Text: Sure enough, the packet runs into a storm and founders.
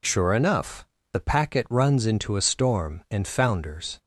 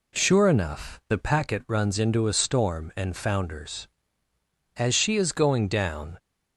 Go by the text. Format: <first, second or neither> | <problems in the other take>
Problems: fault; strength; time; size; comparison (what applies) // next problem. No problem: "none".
first | goes on to say "As she is going down"; from 4.7 s on; 1.4 s long